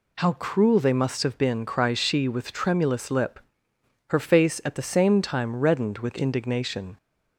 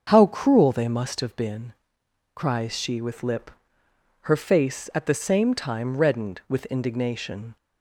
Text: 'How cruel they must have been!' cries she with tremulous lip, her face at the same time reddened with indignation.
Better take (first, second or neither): first